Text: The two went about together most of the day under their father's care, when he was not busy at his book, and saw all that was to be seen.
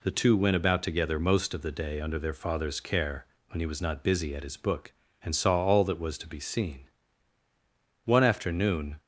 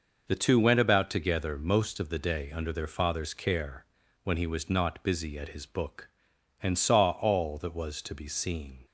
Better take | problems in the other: second | goes on to say "One afternoon"; noticeable; from 8.0 s on; 0.96 s long

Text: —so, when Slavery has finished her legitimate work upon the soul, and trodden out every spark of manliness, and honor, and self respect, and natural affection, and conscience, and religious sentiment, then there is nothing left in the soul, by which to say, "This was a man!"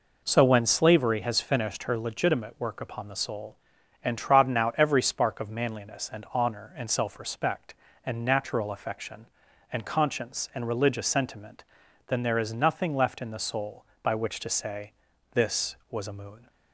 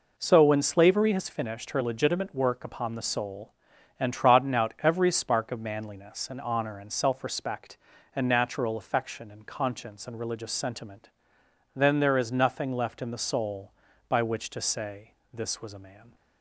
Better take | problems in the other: second | says "moon" for "man"; at 16.1 s

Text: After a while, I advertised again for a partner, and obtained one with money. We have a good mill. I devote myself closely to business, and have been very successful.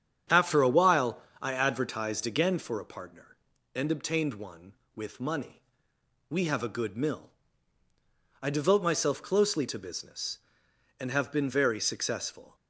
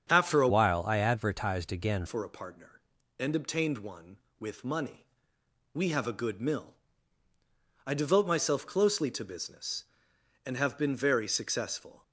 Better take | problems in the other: first | starts louder than the rest; strong; until 1.1 s; 7.5 dB; strong in the first // changes voice from "while" to "again"; from 0.4 to 2.0 s; 1.6 s long

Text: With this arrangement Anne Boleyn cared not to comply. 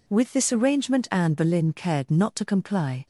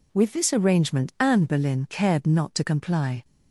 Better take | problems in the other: neither | none

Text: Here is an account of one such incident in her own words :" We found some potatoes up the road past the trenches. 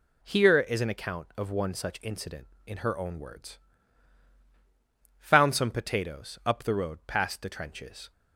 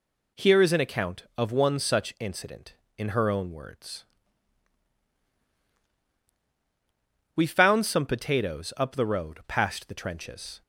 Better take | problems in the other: second | skips "We"; at 5.1 s

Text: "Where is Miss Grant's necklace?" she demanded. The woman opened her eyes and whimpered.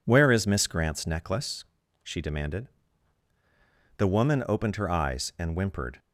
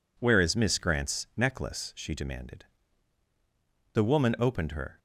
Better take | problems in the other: first | stops before "eyes and whimpered"; at 4.9 s

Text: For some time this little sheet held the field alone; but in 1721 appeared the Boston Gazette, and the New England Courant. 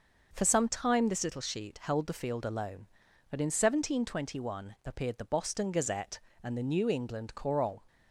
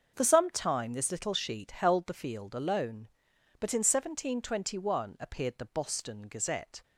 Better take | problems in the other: first | starts louder than the rest; until 1.1 s; 6.5 dB // stops before "and the New England Courant"; at 6.8 s

